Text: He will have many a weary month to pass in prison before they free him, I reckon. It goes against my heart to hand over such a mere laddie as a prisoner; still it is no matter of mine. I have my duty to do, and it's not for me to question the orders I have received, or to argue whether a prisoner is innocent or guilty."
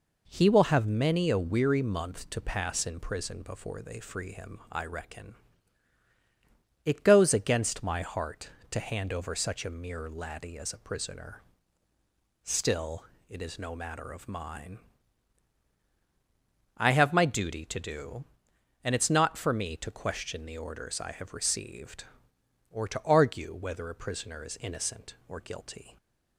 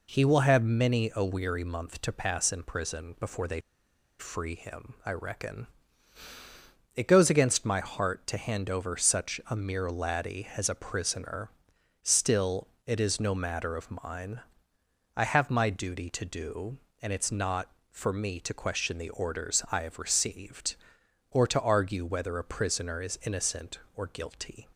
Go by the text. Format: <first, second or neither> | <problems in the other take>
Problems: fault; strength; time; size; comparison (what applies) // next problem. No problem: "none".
first | pauses between "they" and "free"; noticeable; at 3.5 s; 0.59 s long // pauses between "still" and "it"; slight; at 12.6 s; 0.18 s long; slight in the first